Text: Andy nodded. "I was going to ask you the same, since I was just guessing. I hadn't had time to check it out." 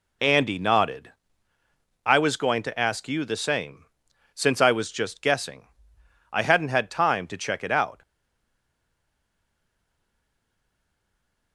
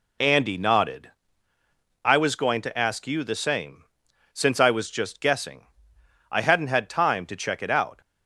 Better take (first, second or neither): second